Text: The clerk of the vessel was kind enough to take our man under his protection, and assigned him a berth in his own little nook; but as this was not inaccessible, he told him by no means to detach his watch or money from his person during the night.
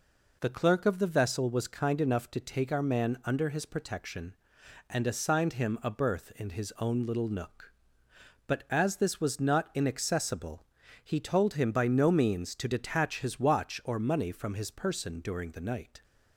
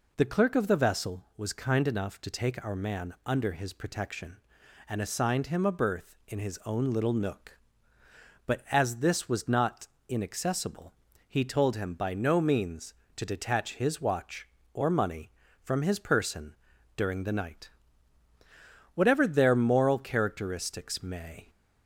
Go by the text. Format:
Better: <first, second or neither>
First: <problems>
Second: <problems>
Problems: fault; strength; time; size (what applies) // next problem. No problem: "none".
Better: first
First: none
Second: pauses between "not" and "inaccessible"; slight; at 9.8 s; 0.22 s long // pauses between "person" and "during"; at 16.5 s; 0.38 s long // goes on to say "Whatever their moral characteristics may"; strong; from 18.9 s on; 2.5 s long